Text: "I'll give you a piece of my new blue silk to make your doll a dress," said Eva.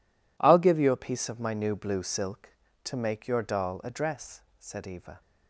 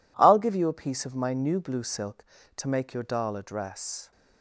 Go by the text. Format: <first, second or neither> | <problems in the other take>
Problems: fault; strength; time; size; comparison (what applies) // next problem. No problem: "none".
first | stops before "said Eva"; at 4.1 s